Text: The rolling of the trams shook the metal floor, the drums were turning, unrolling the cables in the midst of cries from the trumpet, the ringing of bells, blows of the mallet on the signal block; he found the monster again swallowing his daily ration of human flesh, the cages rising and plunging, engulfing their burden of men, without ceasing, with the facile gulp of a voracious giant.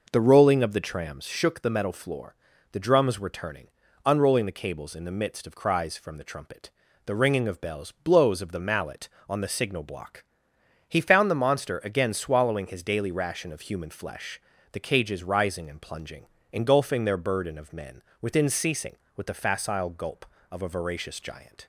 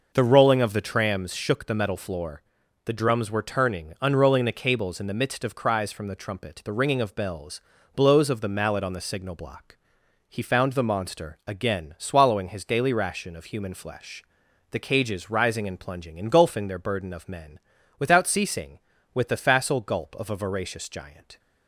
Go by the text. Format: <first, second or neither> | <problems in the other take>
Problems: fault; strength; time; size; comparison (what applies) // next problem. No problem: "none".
second | says "within" for "without"; at 18.2 s